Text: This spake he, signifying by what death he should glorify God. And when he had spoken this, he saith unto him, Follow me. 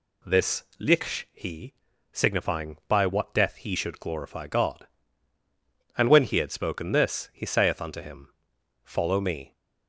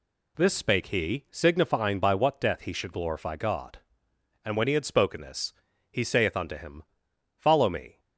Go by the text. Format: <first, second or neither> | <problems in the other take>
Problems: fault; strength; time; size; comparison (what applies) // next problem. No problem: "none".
second | says "liksh" for "spake"; at 0.7 s